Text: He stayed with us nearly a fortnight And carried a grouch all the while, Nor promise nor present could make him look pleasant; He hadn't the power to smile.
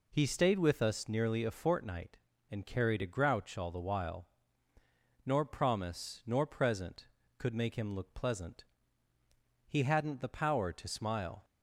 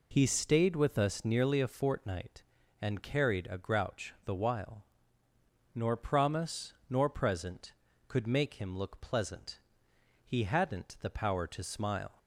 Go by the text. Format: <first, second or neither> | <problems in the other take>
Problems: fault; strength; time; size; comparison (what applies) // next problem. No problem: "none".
first | skips "all"; at 4.1 s // pauses between "promise" and "nor"; slight; at 6.7 s; 0.16 s long